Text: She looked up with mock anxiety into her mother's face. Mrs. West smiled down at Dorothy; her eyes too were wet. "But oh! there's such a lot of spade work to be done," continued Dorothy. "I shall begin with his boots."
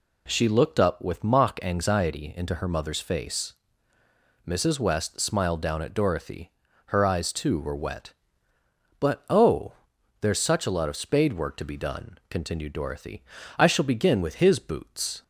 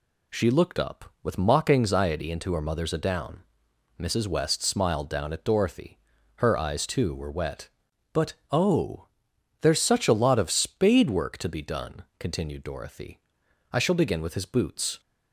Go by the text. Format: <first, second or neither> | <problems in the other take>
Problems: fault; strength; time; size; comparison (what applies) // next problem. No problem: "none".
first | says "adown" for "face"; at 2.9 s // pauses between "But" and "oh"; slight; at 8.3 s; 0.18 s long